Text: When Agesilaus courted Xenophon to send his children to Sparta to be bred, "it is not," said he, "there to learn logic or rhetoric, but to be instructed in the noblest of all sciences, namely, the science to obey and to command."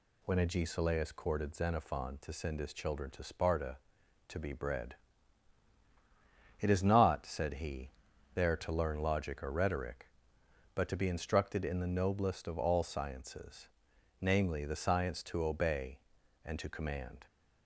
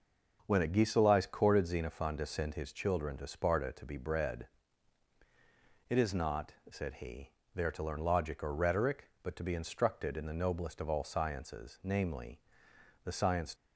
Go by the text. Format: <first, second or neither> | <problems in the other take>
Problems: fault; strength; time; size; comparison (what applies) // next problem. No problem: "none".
first | starts louder than the rest; noticeable; until 1.4 s; 6 dB // stops before "to obey and to command"; at 13.5 s